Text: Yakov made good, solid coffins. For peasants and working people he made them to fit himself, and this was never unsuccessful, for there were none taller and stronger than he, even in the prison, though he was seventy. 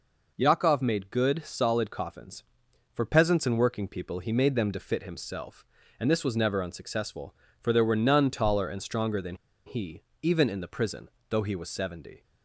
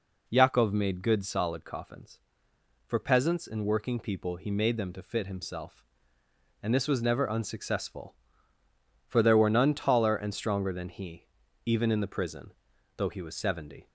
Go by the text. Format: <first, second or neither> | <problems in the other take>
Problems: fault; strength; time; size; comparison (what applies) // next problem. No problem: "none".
second | pauses between "than" and "he"; slight; at 9.3 s; 0.30 s long